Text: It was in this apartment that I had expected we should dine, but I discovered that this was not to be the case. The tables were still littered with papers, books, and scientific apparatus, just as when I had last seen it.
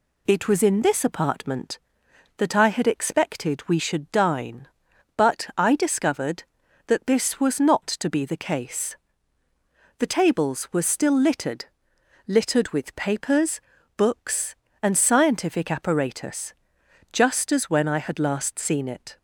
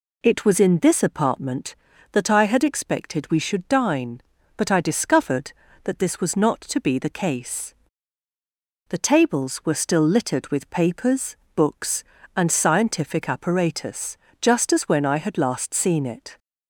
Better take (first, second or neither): second